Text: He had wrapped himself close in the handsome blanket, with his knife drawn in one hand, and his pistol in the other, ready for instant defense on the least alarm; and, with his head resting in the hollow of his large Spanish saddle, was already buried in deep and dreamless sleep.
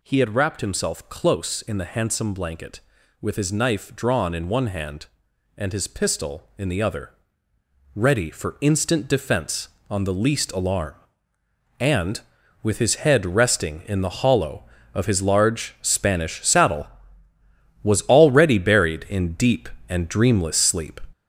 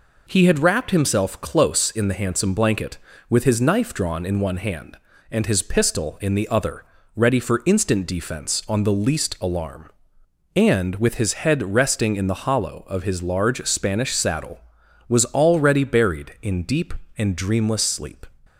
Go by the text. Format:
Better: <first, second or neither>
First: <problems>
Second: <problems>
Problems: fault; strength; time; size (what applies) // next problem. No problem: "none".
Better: second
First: gets louder; noticeable; throughout; 5.5 dB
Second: none